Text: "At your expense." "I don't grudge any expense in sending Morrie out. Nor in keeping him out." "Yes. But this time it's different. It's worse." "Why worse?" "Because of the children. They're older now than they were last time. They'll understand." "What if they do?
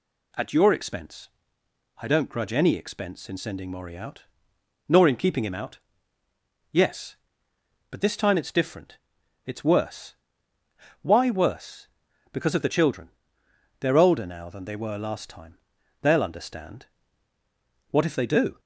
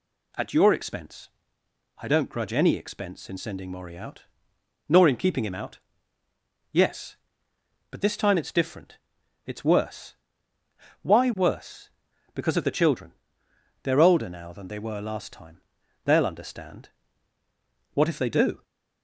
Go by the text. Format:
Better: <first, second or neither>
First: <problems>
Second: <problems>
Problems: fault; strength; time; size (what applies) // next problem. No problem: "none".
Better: neither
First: none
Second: none